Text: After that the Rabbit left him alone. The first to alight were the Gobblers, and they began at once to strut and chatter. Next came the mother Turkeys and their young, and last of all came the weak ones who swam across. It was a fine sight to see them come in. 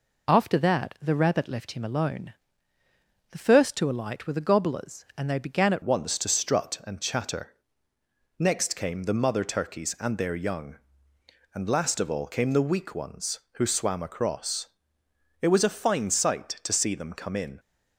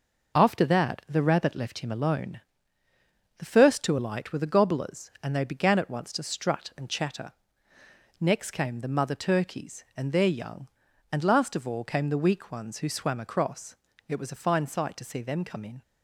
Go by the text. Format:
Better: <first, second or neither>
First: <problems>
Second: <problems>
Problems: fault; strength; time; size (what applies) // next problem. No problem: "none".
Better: second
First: changes voice at "once"; from 5.8 s on; 11.7 s long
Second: none